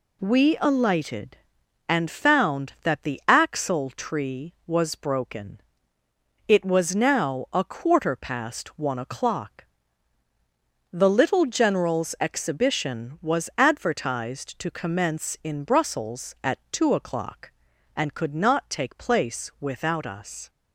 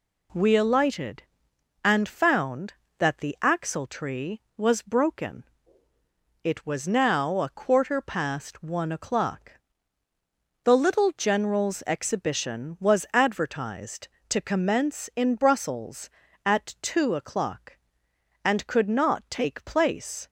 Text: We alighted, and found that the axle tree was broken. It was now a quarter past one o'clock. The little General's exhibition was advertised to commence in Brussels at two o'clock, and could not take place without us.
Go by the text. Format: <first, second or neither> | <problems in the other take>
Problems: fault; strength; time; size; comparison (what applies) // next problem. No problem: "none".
first | stops before "without us"; at 20.2 s